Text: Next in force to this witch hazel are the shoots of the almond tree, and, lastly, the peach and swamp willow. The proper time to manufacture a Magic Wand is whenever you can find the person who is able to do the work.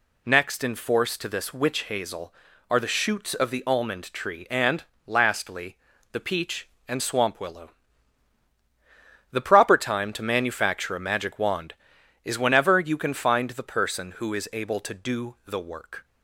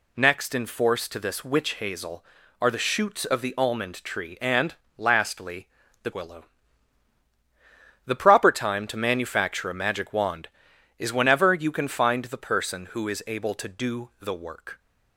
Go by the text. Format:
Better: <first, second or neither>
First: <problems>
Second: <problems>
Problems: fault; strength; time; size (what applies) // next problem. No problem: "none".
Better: first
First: none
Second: skips "peach and swamp"; at 6.1 s